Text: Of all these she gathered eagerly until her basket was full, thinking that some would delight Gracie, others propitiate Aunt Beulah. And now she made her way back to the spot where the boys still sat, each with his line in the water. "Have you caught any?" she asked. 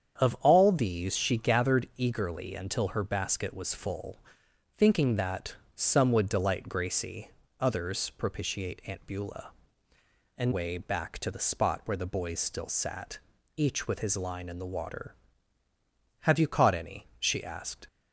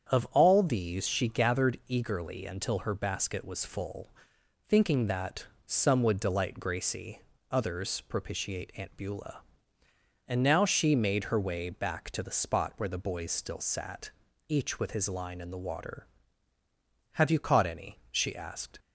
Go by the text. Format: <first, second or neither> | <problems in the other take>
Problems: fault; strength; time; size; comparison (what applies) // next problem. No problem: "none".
second | starts louder than the rest; strong; until 1.2 s; 8 dB; strong in the second // pauses between "that" and "some"; slight; at 5.5 s; 0.20 s long; slight in the second // skips "now she made her"; at 10.5 s